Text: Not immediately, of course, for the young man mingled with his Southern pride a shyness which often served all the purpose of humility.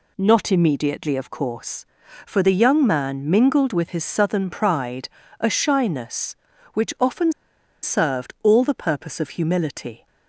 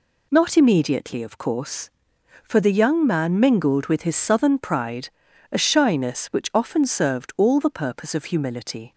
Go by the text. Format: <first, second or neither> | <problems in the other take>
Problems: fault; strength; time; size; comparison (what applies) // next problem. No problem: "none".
second | pauses between "pride" and "a"; slight; at 5.0 s; 0.32 s long; also in the second // pauses between "often" and "served"; noticeable; at 7.3 s; 0.50 s long